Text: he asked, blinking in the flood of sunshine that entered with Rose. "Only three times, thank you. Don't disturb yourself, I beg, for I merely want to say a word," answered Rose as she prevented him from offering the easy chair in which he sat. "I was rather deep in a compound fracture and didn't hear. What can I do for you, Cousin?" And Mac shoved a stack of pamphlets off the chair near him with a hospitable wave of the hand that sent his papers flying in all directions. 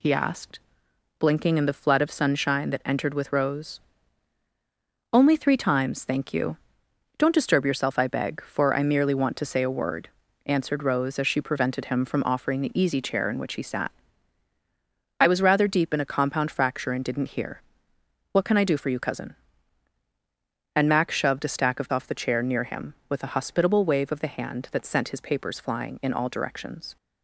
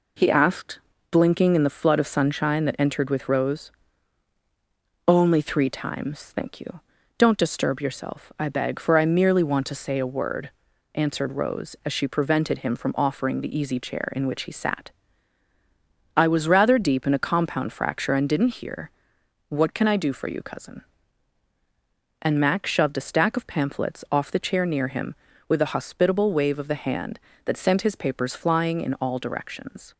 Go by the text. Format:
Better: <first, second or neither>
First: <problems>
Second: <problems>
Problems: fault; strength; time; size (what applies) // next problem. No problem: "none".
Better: second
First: skips "pamphlets"; at 21.9 s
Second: none